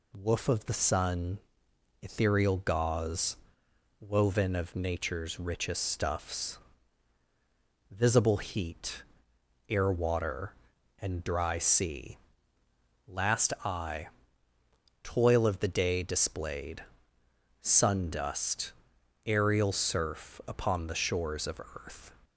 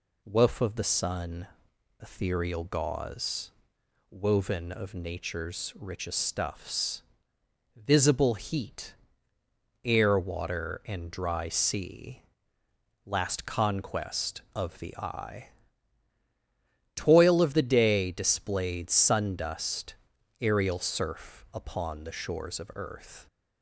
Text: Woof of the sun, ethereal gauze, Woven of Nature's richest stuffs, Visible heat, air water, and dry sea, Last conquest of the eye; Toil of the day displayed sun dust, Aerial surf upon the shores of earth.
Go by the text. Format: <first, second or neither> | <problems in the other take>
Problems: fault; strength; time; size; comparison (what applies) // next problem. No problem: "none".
second | skips "conquest of the"; at 13.5 s // pauses between "displayed" and "sun"; noticeable; at 16.8 s; 0.80 s long